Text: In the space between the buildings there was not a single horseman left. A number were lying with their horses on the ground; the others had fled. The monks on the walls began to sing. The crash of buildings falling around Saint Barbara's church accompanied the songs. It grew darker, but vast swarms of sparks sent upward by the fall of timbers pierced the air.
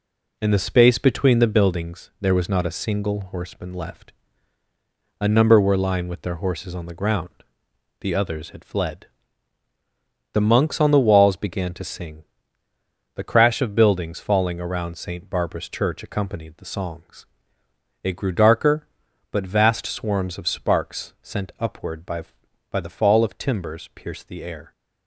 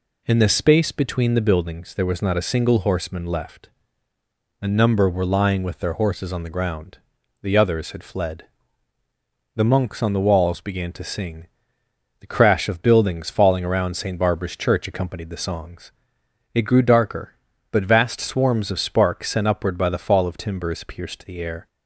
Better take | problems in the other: second | says "by" twice; at 22.6 s

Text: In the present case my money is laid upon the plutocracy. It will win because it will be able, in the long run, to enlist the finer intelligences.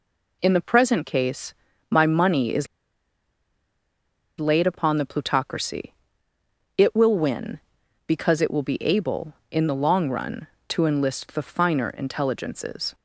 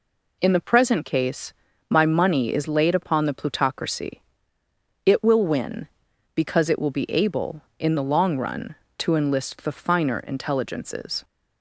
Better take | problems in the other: second | pauses between "case" and "my"; at 1.5 s; 0.38 s long; also in the second // pauses between "is" and "laid"; strong; at 2.6 s; 1.7 s long

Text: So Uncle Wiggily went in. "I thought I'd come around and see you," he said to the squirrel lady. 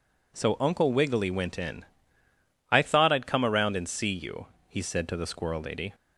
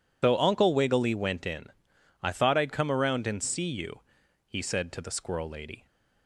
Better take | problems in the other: first | loses the start of "So"; at 0.2 s; 90 ms

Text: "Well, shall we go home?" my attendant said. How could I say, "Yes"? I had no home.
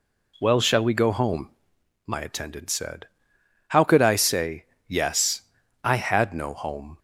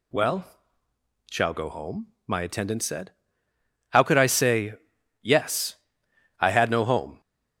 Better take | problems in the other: first | skips "we"; at 1.5 s

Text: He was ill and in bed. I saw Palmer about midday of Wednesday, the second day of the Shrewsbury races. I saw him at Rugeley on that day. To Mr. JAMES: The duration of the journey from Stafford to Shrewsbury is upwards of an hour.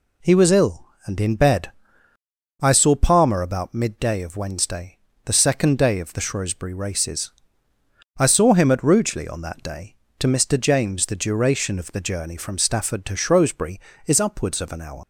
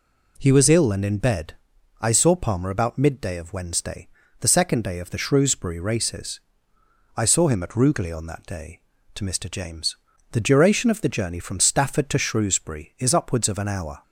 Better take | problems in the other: second | leaves "hour" unfinished; at 15.0 s; 100 ms

